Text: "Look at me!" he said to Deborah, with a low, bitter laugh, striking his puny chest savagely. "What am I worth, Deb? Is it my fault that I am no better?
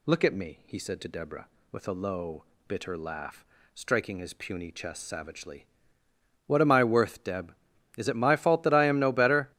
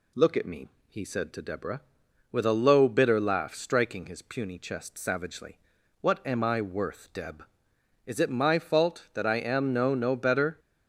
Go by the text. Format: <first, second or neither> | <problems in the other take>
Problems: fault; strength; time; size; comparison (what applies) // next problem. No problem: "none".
first | says "no" twice; at 9.9 s